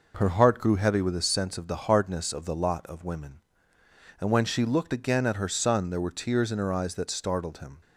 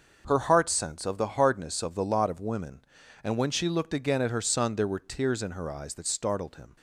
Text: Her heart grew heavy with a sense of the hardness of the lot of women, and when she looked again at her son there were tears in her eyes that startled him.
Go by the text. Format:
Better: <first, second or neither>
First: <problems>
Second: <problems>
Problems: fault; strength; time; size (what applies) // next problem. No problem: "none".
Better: first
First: none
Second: starts louder than the rest; noticeable; until 1.2 s; 6 dB // skips "grew heavy with a"; at 0.6 s